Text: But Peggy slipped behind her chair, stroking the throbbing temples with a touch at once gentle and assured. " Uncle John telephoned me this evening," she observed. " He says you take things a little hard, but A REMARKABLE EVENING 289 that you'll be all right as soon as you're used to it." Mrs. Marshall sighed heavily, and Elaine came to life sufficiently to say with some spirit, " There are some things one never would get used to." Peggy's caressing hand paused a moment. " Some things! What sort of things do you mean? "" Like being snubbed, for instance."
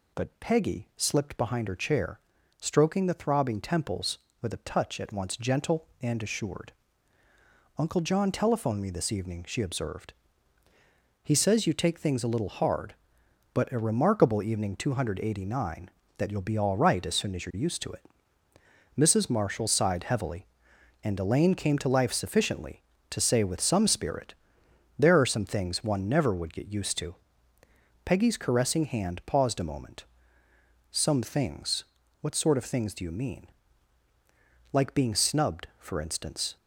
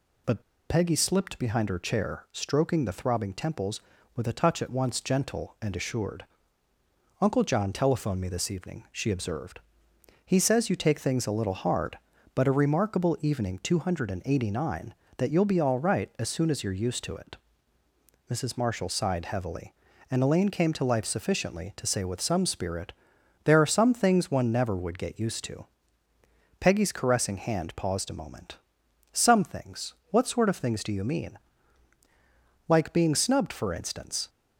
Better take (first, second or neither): first